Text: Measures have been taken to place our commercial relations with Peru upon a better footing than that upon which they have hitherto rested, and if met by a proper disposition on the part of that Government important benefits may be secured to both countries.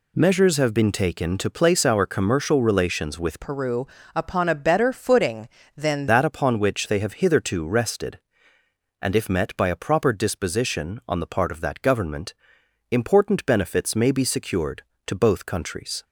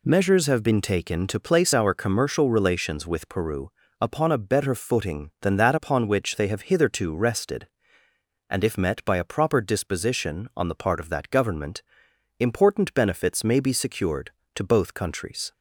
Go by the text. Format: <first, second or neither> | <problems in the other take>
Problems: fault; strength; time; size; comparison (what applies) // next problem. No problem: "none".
second | changes voice from "Peru" to "than"; from 3.4 to 6.0 s; 2.6 s long // pauses between "Peru" and "upon"; slight; at 3.8 s; 0.28 s long; slight in the second // pauses between "Government" and "important"; noticeable; at 12.3 s; 0.56 s long; noticeable in the second